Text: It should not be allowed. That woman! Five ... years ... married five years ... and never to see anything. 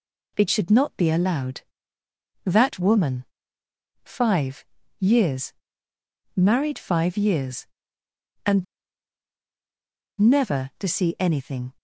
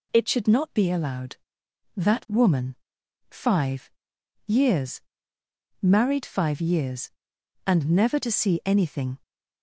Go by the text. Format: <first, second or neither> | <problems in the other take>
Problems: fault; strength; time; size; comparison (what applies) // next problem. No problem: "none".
second | pauses between "and" and "never"; strong; at 8.6 s; 1.5 s long